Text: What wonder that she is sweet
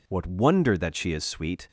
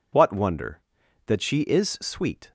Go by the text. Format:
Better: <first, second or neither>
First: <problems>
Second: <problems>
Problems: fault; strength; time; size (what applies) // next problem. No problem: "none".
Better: neither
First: none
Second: none